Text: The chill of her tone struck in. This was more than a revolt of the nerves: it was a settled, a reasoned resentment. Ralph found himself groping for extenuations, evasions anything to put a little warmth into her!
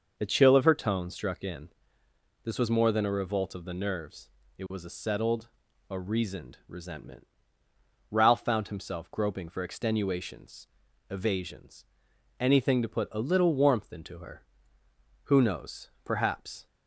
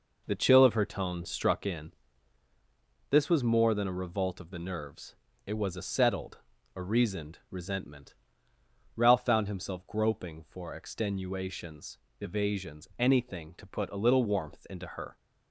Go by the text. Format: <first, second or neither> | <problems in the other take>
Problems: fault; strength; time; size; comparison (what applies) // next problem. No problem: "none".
second | starts louder than the rest; noticeable; until 1.1 s; 6 dB // pauses between "evasions" and "anything"; noticeable; at 11.8 s; 0.52 s long // goes on to say "Who knows Perhaps"; from 15.2 s on; 1.3 s long